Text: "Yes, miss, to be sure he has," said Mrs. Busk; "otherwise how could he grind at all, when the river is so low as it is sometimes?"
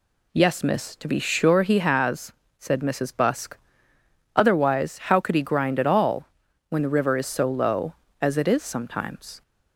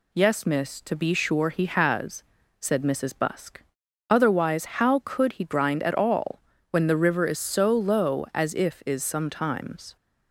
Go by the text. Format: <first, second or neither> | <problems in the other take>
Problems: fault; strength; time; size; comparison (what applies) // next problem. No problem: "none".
first | says "if" for "it"; at 8.5 s